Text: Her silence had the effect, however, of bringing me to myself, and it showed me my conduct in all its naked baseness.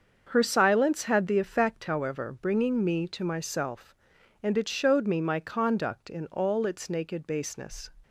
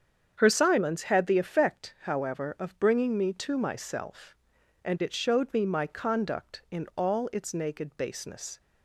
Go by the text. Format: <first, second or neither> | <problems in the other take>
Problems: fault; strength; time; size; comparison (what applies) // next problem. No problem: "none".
second | starts louder than the rest; until 1.3 s; 7 dB; strong in the second // skips "of"; at 2.3 s